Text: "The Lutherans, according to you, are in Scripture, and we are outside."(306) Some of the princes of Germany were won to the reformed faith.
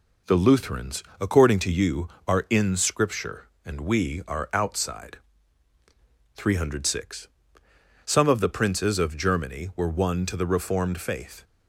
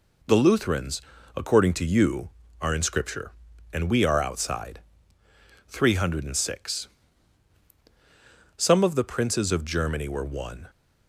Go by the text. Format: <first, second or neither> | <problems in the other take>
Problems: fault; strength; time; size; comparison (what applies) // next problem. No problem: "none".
first | stops before "to the reformed faith"; at 10.6 s